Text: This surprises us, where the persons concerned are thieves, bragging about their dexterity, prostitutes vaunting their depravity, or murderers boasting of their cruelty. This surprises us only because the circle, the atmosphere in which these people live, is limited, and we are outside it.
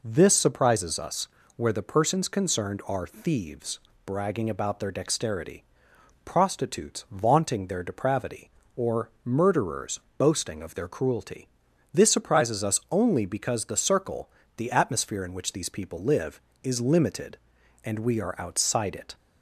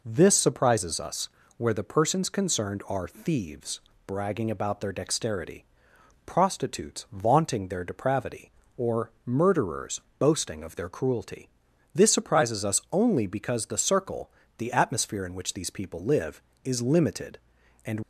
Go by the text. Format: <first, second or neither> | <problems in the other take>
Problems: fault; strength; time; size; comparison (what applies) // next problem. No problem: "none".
first | pauses between "murderers" and "boasting"; slight; at 10.0 s; 0.18 s long; slight in the first // stops before "we are outside it"; at 18.0 s